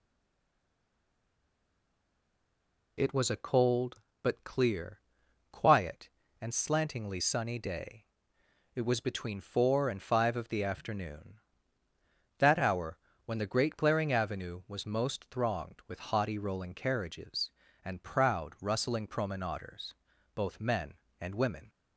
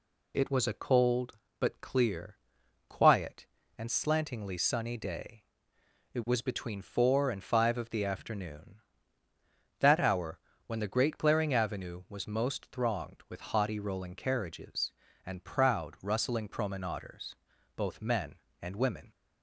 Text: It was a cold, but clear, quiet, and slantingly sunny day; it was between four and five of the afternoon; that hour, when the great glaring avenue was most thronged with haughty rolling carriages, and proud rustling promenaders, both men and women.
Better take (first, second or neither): second